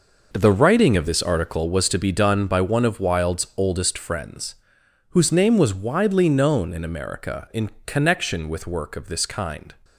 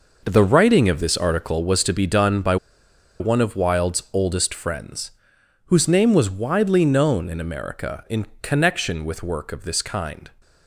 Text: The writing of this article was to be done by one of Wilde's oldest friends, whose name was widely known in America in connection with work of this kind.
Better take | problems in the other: first | pauses between "by" and "one"; noticeable; at 2.5 s; 0.64 s long // pauses between "in" and "connection"; slight; at 8.2 s; 0.16 s long; slight in the first

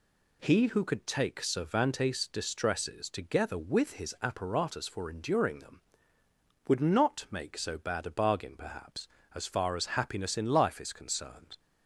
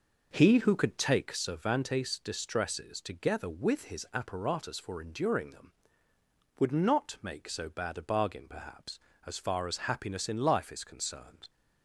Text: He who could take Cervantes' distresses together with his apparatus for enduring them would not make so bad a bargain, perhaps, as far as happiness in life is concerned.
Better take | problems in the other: first | starts louder than the rest; noticeable; until 1.3 s; 5.5 dB

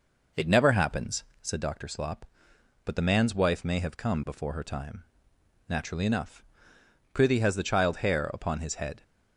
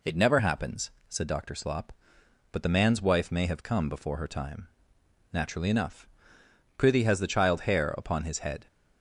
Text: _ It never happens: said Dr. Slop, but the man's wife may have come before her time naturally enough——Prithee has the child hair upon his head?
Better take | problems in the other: second | starts louder than the rest; noticeable; until 1.5 s; 5 dB // pauses between "time" and "naturally"; noticeable; at 5.0 s; 0.64 s long; noticeable in the second

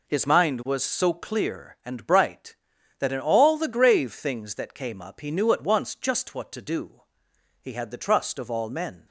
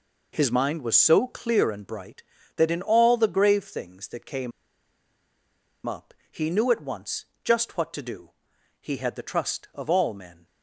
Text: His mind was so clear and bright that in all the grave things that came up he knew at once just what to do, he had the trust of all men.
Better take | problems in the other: first | pauses between "came" and "up"; strong; at 4.5 s; 1.3 s long // pauses between "up" and "he"; slight; at 6.1 s; 0.18 s long // pauses between "once" and "just"; slight; at 7.2 s; 0.18 s long

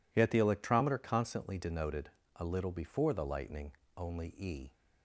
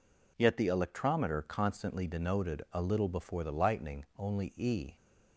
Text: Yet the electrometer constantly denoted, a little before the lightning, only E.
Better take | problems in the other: neither | none

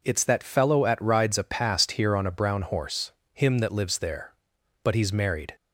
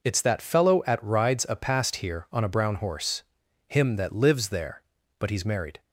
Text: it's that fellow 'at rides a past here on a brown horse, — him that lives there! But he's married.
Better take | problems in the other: neither | none

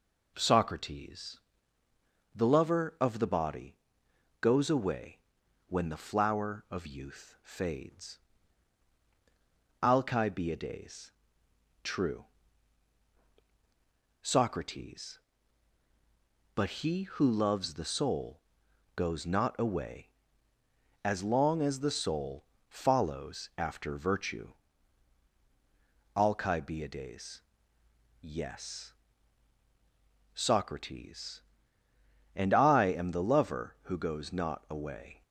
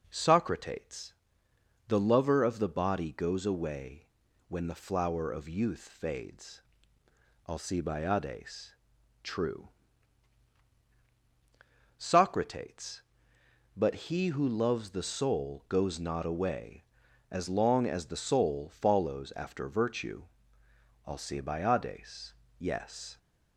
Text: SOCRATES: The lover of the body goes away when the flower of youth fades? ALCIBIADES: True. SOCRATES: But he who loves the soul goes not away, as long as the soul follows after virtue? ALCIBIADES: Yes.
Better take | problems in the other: second | pauses between "body" and "goes"; noticeable; at 3.7 s; 0.64 s long // pauses between "away" and "when"; noticeable; at 5.1 s; 0.48 s long; also in the second // pauses between "soul" and "goes"; noticeable; at 18.3 s; 0.56 s long // pauses between "soul" and "follows"; slight; at 22.4 s; 0.24 s long // goes on to say "SOCRATES And I am the lover who goes not away"; strong; from 30.3 s on; 4.8 s long

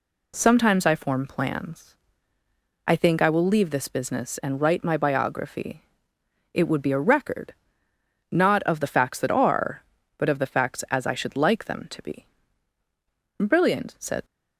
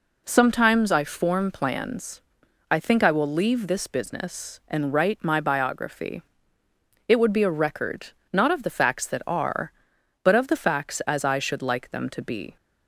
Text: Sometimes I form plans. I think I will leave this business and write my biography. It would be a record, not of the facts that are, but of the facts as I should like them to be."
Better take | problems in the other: second | goes on to say "Brilliant said"; noticeable; from 13.3 s on; 0.86 s long

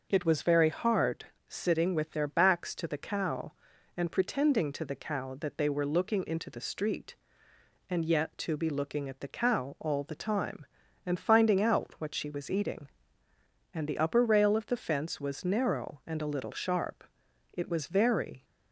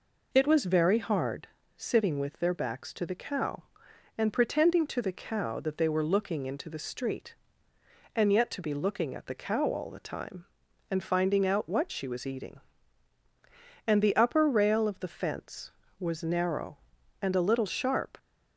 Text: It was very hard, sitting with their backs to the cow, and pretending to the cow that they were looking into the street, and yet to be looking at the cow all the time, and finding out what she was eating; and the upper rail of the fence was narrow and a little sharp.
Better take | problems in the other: second | goes on to say "It was very"; noticeable; from 17.5 s on; 0.92 s long

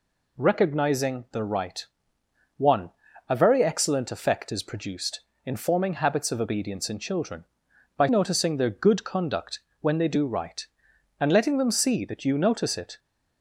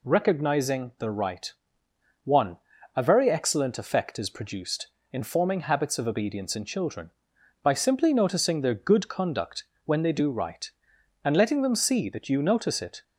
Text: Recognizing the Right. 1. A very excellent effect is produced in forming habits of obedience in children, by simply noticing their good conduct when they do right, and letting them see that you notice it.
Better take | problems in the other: second | skips "simply"; at 8.0 s // pauses between "conduct" and "when"; slight; at 9.6 s; 0.20 s long; slight in the second

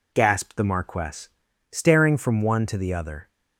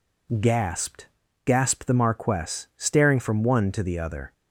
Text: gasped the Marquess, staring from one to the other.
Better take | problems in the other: first | says "gasped" twice; at 1.4 s

